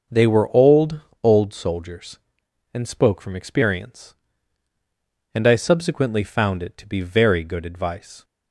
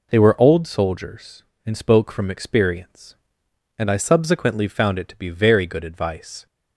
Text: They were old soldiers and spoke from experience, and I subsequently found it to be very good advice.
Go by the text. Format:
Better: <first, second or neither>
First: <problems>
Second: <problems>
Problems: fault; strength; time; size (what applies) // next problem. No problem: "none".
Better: second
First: starts louder than the rest; noticeable; until 1.3 s; 6 dB // says "old" twice; at 1.2 s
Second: none